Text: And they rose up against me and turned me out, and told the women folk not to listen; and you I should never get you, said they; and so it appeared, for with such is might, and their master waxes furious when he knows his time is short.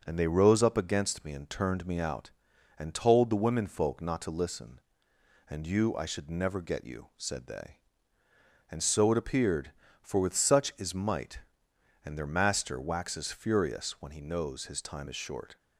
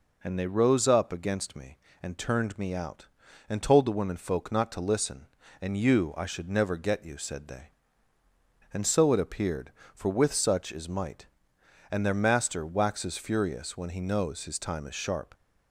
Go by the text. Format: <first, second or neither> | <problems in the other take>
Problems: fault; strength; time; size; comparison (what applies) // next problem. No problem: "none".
first | says "sharp" for "short"; at 14.9 s